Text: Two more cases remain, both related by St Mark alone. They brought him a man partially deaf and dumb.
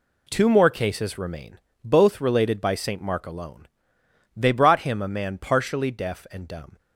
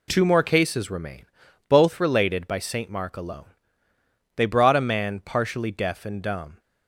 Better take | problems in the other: first | skips "him"; at 4.7 s

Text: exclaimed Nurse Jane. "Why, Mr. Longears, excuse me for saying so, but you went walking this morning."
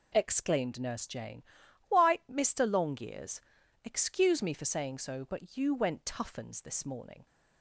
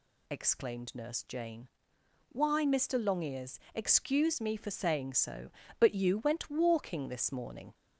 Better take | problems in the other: second | says "toughens" for "walking"; at 6.0 s

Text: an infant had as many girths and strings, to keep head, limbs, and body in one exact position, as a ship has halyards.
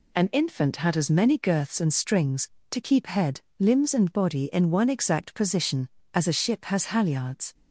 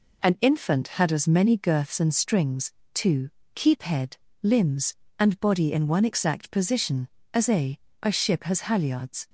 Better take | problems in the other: first | pauses between "to" and "keep"; slight; at 3.2 s; 0.26 s long // says "a" twice; at 8.0 s

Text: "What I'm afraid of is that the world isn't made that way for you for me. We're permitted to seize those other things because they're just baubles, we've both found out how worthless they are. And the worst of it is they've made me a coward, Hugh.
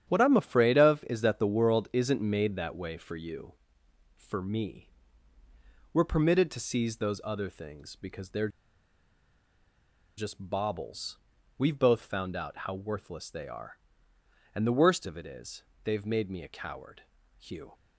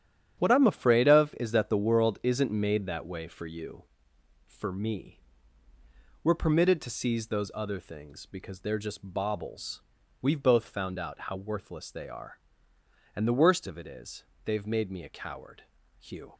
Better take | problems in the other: second | starts louder than the rest; strong; until 1.0 s; 9 dB; strong in the second // pauses between "they're" and "just"; strong; at 8.4 s; 1.6 s long // pauses between "is" and "they've"; slight; at 15.6 s; 0.20 s long; slight in the second

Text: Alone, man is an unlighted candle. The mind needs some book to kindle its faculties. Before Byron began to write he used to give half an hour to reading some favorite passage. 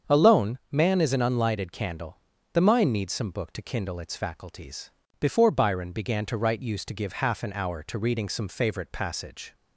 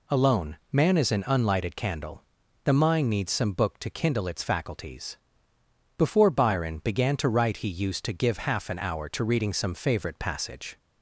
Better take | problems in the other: second | starts louder than the rest; strong; until 1.1 s; 7 dB // skips "he"; at 6.6 s

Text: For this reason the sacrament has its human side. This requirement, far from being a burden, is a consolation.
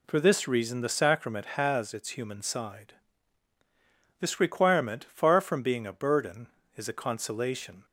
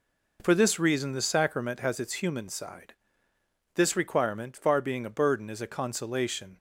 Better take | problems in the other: first | skips "from"; at 4.8 s

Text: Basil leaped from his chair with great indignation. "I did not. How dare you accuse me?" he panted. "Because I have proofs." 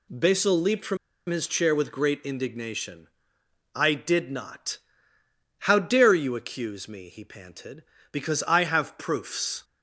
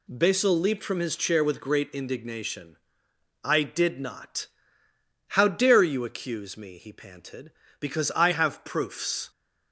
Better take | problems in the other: second | pauses between "from" and "his"; slight; at 0.9 s; 0.32 s long

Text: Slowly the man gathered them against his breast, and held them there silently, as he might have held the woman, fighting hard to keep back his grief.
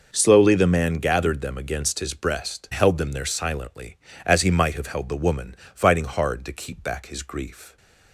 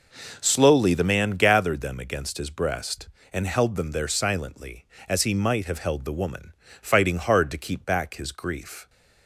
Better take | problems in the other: second | skips "and"; at 2.7 s

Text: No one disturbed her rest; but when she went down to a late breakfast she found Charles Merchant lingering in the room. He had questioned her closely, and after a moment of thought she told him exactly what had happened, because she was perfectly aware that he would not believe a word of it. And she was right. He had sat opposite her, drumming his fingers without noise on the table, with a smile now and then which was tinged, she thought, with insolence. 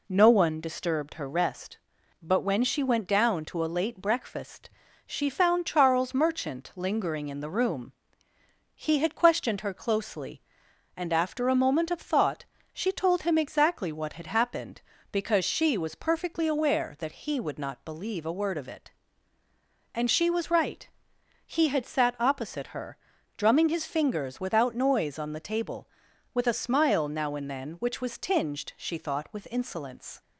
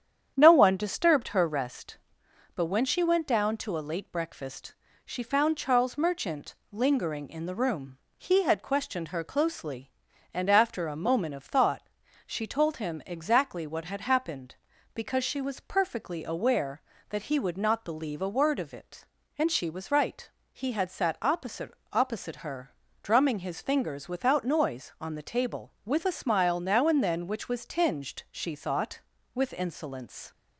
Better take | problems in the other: first | starts louder than the rest; strong; until 1.3 s; 9 dB // pauses between "breakfast" and "she"; slight; at 4.7 s; 0.30 s long; also in the first // pauses between "Merchant" and "lingering"; slight; at 6.5 s; 0.18 s long // pauses between "thought" and "she"; at 11.8 s; 0.44 s long; slight in the first // says "opposite" twice; at 21.9 s

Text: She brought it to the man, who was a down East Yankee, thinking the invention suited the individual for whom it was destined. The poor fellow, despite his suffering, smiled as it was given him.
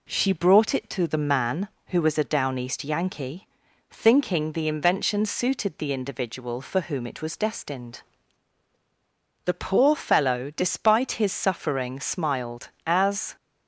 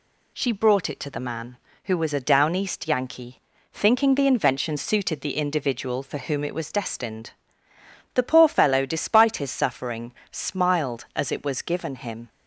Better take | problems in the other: second | stops before "it was given him"; at 13.3 s

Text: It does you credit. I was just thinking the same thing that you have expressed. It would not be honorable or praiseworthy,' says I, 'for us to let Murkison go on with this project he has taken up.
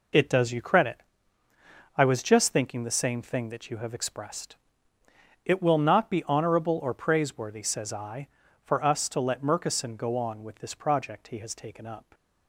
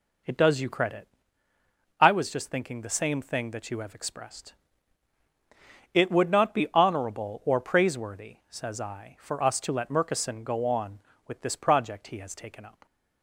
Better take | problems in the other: second | says "will" for "would"; at 5.5 s

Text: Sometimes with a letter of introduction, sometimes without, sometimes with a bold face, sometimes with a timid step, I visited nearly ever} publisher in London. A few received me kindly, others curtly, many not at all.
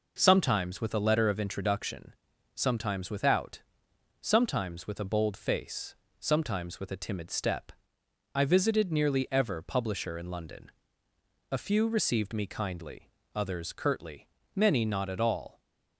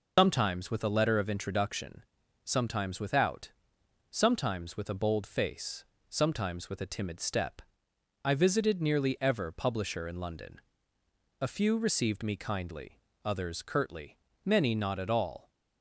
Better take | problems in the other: first | loses the start of "Sometimes"; at 0.1 s; 120 ms

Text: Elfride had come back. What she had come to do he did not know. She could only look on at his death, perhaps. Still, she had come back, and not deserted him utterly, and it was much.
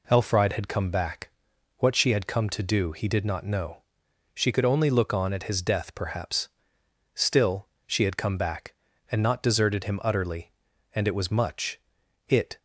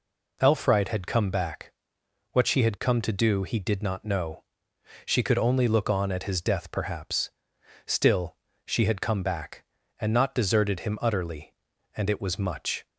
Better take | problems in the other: second | goes on to say "It"; slight; from 12.2 s on; 0.30 s long

